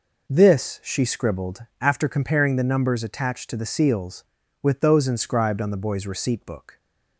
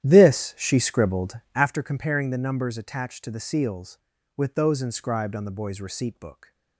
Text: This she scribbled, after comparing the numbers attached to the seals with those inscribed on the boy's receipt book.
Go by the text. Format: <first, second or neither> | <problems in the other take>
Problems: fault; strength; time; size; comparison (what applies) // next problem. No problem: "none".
first | starts louder than the rest; strong; until 1.8 s; 11.5 dB